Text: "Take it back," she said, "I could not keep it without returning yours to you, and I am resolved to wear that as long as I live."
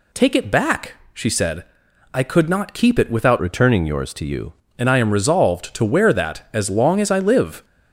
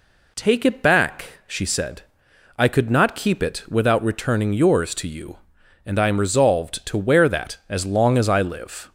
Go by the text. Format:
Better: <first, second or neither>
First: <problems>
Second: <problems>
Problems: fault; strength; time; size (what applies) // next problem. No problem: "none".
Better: second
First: changes voice from "returning" to "you"; from 3.3 to 4.5 s; 1.2 s long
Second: none